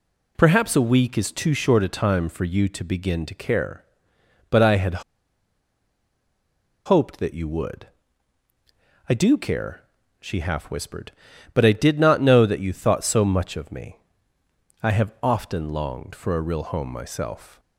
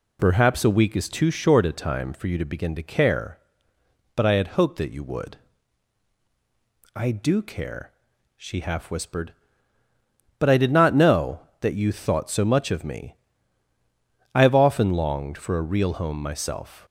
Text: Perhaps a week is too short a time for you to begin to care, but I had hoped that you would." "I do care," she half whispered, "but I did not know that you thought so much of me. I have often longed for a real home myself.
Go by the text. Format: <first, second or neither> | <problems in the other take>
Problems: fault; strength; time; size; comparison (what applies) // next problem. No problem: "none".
second | pauses between "had" and "hoped"; strong; at 5.0 s; 1.8 s long